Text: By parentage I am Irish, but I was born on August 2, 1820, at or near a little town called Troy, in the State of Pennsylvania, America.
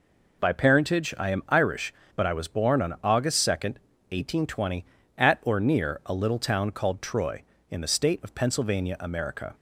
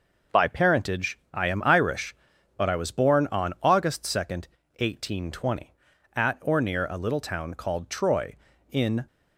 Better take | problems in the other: first | pauses between "parentage" and "I"; slight; at 1.1 s; 0.16 s long // stops before "the State of Pennsylvania America"; at 9.0 s

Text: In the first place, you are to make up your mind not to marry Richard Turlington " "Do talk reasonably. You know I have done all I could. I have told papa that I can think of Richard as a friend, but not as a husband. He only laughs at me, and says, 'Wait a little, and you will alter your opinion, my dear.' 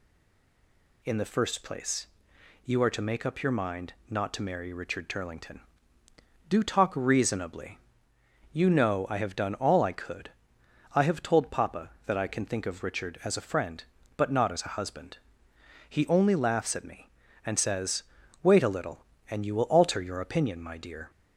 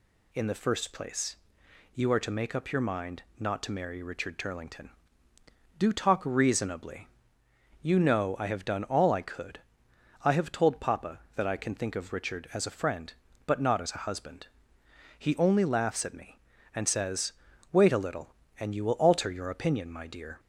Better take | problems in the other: second | stays silent before the first word; until 1.0 s; 1.0 s long

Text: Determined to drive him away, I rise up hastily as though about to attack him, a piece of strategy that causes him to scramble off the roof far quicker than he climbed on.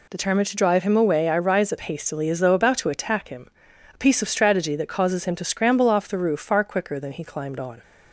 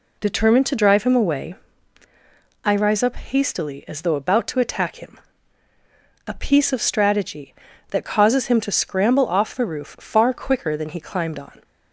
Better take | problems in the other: neither | none

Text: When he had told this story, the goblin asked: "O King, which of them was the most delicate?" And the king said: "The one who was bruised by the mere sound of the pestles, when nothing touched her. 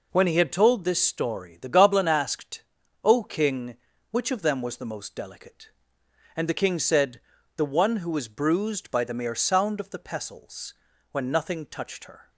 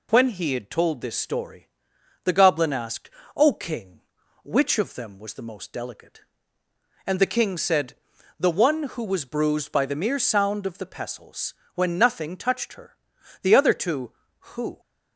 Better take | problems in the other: first | goes on to say "The other two who"; from 13.4 s on; 1.3 s long

